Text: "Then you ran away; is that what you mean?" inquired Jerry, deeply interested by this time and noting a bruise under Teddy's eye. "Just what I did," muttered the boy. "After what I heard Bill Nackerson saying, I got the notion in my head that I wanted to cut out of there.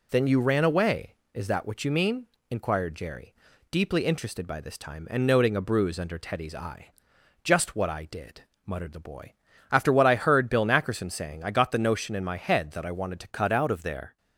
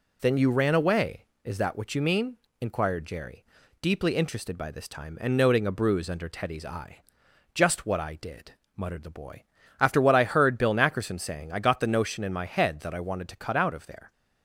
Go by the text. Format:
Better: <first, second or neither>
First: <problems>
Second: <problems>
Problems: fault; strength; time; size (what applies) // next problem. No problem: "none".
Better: second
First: changes voice at "cut"; from 13.3 s on; 0.8 s long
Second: none